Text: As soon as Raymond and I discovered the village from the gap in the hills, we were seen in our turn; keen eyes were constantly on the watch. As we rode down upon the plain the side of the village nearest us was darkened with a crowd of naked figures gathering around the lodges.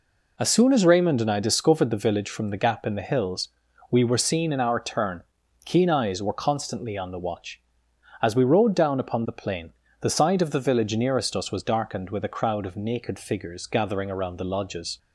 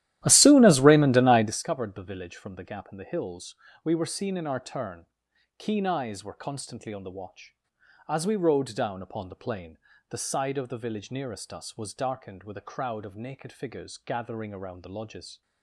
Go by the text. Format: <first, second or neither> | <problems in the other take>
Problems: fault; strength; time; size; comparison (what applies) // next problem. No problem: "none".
first | starts louder than the rest; strong; until 1.5 s; 13.5 dB // pauses between "plain" and "the"; slight; at 9.7 s; 0.32 s long; slight in the first